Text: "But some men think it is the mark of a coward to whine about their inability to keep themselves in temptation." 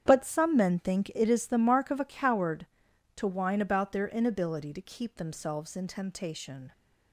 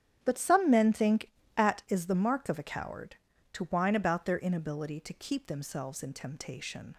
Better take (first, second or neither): first